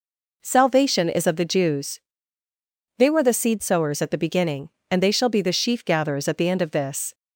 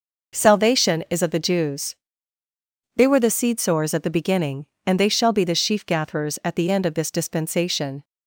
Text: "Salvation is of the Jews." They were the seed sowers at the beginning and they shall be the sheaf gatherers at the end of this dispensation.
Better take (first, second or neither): second